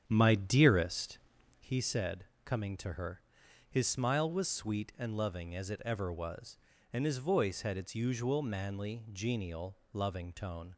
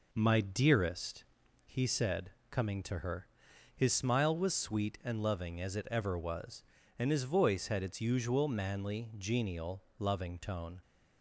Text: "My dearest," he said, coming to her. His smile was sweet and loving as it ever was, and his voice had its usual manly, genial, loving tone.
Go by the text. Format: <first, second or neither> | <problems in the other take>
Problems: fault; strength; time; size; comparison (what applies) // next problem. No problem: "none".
second | starts louder than the rest; strong; until 1.8 s; 8.5 dB